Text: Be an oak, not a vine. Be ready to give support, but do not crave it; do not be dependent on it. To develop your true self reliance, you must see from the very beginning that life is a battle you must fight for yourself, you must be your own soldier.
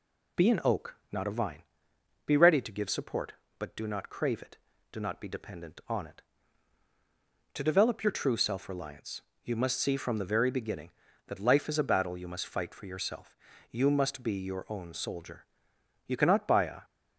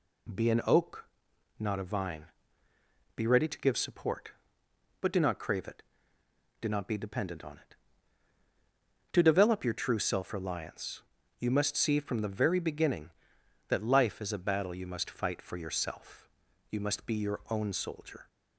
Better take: second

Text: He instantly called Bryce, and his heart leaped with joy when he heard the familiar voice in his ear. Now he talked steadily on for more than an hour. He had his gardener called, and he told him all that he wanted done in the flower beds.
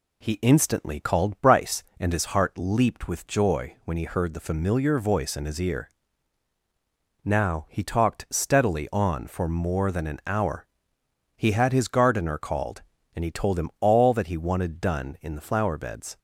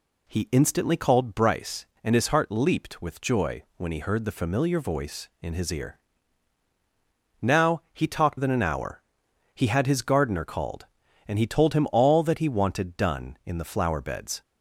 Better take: first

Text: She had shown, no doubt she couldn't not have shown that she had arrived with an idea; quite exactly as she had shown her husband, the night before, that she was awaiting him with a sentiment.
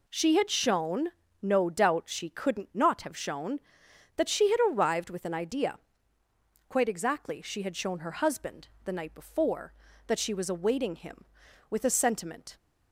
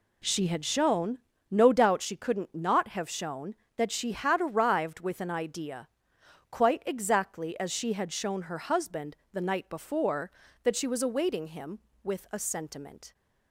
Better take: second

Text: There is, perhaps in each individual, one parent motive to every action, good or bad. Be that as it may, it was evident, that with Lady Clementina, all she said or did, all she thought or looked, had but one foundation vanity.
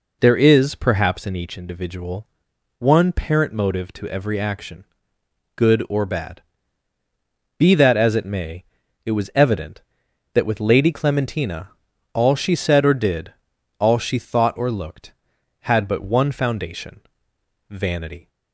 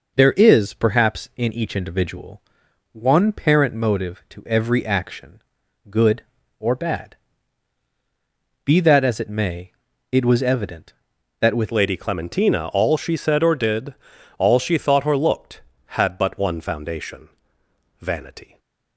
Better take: first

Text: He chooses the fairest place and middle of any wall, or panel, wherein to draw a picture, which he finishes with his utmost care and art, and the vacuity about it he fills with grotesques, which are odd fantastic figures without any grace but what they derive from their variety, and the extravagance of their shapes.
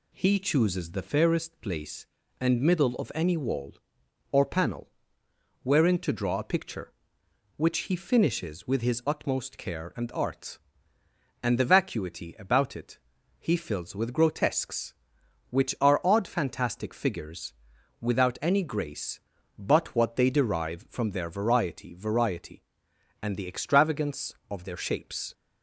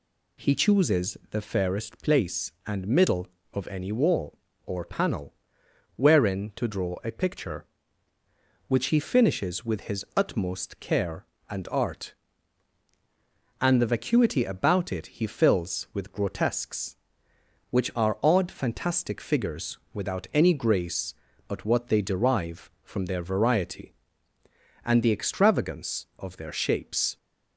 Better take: second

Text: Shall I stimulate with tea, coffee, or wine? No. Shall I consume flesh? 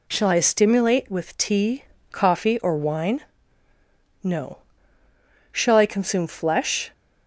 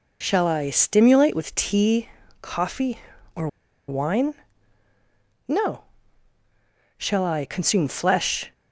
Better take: first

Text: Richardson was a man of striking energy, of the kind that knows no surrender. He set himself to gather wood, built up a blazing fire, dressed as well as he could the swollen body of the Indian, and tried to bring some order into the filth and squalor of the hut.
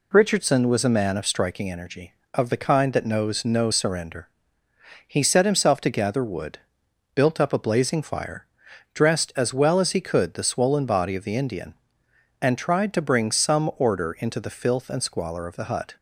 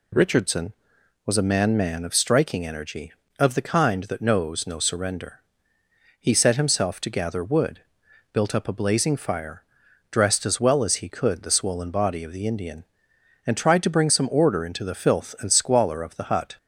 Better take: first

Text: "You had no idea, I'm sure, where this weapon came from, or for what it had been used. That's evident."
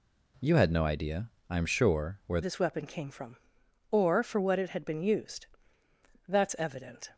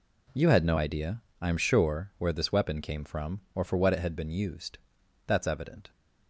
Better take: second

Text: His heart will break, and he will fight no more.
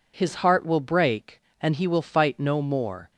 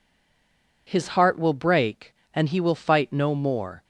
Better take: first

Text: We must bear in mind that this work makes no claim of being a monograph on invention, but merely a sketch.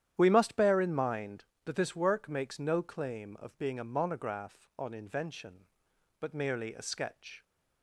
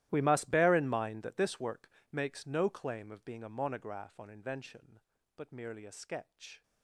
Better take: first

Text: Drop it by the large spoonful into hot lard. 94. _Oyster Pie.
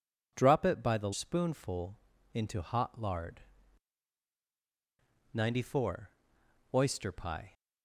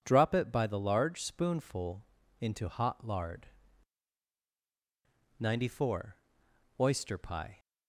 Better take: second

